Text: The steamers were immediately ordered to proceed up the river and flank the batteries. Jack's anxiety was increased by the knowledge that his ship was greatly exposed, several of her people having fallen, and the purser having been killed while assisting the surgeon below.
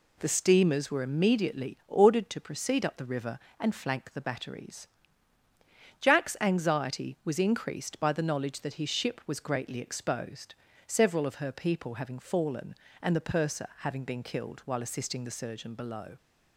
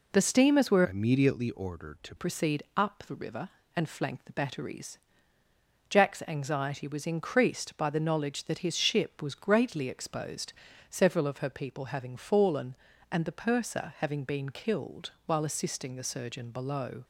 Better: first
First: none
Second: changes voice from "immediately" to "to"; from 0.8 to 2.1 s; 1.3 s long // pauses between "killed" and "while"; slight; at 15.1 s; 0.16 s long

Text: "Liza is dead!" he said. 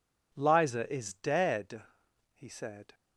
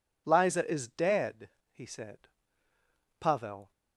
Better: first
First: none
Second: goes on to say "Pavel"; from 3.2 s on; 0.50 s long

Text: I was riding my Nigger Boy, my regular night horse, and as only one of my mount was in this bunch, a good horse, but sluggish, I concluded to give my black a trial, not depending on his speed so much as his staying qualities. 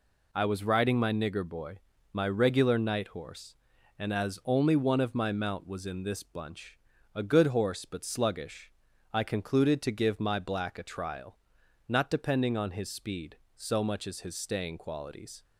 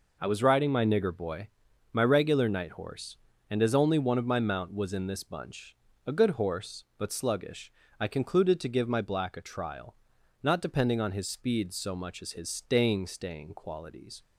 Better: first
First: none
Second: says "staying" twice; at 13.0 s

